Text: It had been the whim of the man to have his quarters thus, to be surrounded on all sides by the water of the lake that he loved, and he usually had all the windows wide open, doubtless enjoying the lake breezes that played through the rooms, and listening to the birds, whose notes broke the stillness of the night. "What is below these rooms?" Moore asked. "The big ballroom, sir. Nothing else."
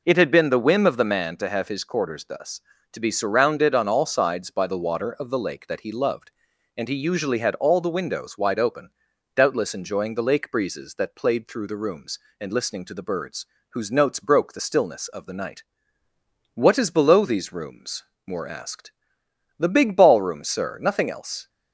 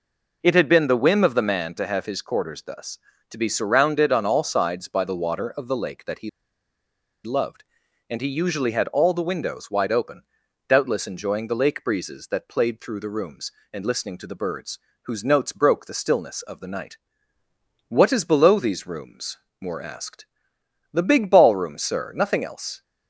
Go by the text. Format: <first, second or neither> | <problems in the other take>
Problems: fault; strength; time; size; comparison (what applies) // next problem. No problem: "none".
first | pauses between "he" and "loved"; noticeable; at 6.2 s; 0.94 s long